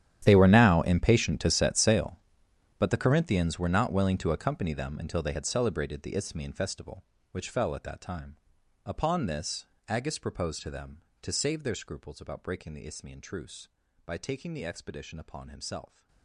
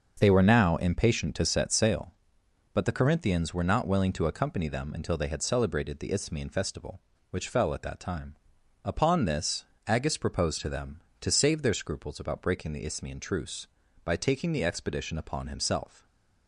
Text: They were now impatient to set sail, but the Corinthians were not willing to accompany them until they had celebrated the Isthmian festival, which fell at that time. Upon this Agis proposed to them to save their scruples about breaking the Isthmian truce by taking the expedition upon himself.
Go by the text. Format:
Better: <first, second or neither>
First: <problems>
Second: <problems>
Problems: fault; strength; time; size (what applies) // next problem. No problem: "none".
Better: second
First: gets quieter; strong; throughout; 19.5 dB // starts louder than the rest; strong; until 1.2 s; 10.5 dB // pauses between "this" and "Agis"; slight; at 9.6 s; 0.22 s long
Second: starts louder than the rest; until 1.2 s; 6.5 dB // pauses between "this" and "Agis"; slight; at 9.6 s; 0.22 s long